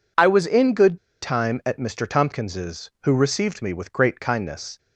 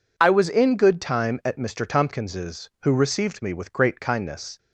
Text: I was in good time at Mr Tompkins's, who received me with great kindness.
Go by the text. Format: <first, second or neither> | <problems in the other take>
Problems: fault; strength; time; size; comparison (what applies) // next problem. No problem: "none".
second | pauses between "good" and "time"; slight; at 0.9 s; 0.26 s long